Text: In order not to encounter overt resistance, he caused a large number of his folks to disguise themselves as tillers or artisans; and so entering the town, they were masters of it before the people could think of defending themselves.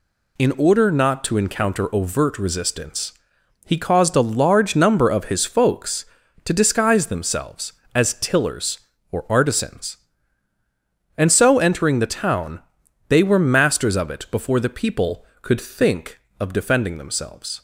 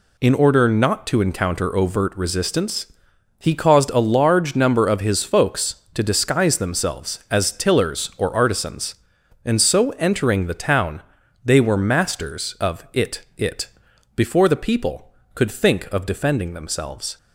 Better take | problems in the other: first | says "it" twice; at 13.3 s

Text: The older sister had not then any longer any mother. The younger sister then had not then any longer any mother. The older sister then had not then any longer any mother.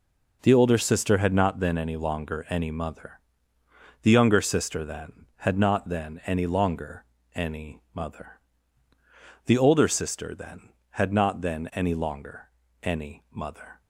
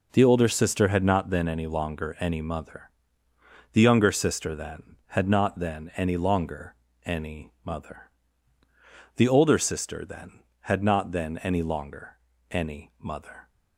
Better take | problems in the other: neither | pauses between "longer" and "any"; slight; the same in both // pauses between "longer" and "any"; slight; the same in both

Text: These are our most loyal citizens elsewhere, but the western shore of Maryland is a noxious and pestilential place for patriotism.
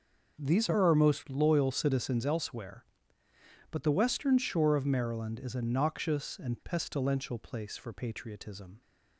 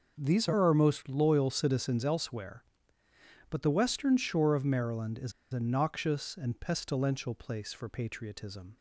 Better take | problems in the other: first | pauses between "is" and "a"; slight; at 5.3 s; 0.20 s long

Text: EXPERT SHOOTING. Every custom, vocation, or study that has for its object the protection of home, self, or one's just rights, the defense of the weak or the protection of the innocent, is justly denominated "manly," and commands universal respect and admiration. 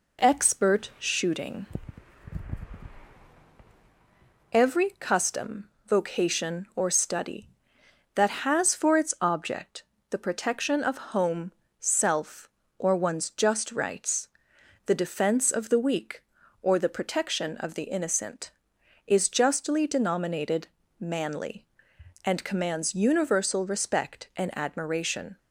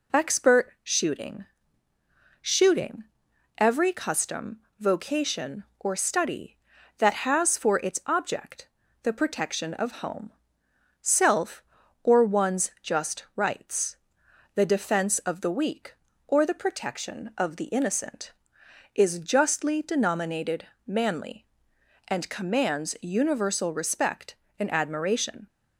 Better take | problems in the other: first | says "SHOOTING" twice; at 2.4 s // pauses between "object" and "the"; at 8.6 s; 0.38 s long; slight in the first // pauses between "denominated" and "manly"; slight; at 20.6 s; 0.22 s long; slight in the first

